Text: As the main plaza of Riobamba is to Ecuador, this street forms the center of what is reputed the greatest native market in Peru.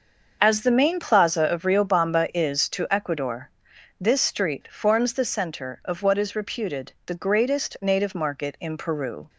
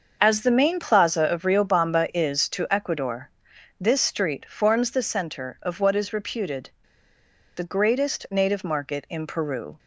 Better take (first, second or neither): first